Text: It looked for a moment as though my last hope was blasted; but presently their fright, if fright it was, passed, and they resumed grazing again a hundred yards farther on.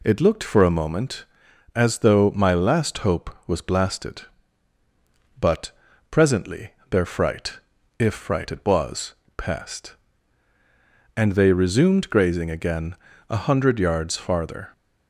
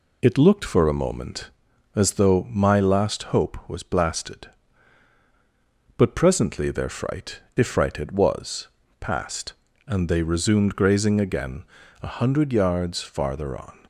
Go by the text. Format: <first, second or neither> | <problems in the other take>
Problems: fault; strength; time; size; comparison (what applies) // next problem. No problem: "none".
second | pauses between "but" and "presently"; at 5.7 s; 0.40 s long // pauses between "presently" and "their"; slight; at 6.7 s; 0.20 s long // pauses between "again" and "a"; slight; at 12.9 s; 0.32 s long; slight in the second // stops before "on"; at 14.7 s